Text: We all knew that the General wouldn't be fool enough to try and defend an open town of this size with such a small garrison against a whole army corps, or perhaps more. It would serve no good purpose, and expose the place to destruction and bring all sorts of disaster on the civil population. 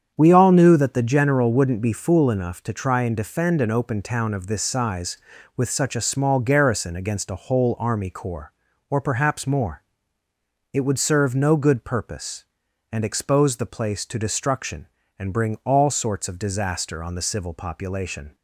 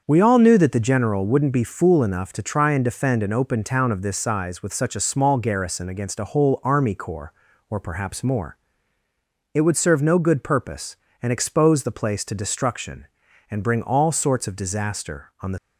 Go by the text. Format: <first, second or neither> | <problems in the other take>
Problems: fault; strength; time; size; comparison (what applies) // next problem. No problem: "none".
first | starts louder than the rest; until 1.0 s; 6.5 dB; strong in the first // stops before "civil population"; at 15.5 s